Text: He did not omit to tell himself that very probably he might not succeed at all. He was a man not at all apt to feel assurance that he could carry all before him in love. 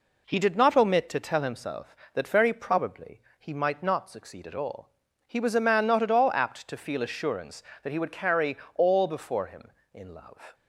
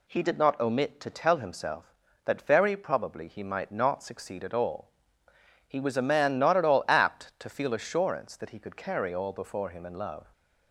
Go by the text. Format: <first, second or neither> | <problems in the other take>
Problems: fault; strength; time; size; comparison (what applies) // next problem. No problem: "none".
second | pauses between "probably" and "he"; slight; at 3.2 s; 0.18 s long // says "would" for "could"; at 7.9 s // pauses between "carry" and "all"; slight; at 8.5 s; 0.20 s long